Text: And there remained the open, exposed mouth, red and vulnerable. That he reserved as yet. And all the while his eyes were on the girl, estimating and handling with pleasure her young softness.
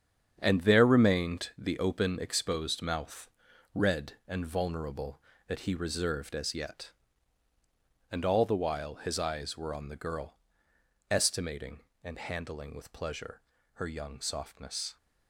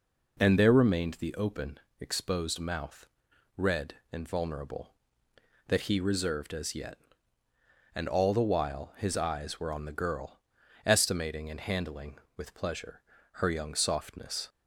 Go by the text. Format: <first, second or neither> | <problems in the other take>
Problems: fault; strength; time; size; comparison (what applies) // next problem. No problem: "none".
second | gets quieter; strong; throughout; 8.5 dB // pauses between "pleasure" and "her"; slight; at 13.3 s; 0.36 s long; slight in the second